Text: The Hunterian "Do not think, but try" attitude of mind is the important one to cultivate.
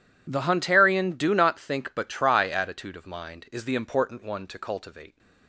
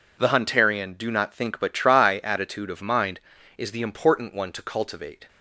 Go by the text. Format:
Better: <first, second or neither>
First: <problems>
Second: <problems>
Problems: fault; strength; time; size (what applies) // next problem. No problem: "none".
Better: neither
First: none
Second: none